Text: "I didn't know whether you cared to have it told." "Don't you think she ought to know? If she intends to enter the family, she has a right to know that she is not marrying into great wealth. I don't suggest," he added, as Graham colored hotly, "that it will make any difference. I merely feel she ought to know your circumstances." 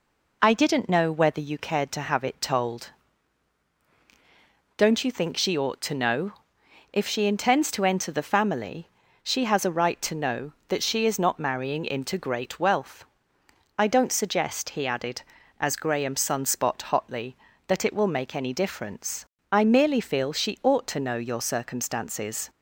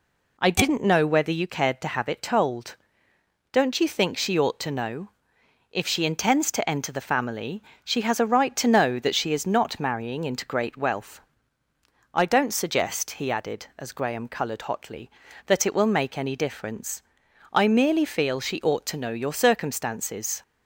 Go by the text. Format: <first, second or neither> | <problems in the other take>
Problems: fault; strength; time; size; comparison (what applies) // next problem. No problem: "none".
second | says "sunspot" for "colored"; at 16.1 s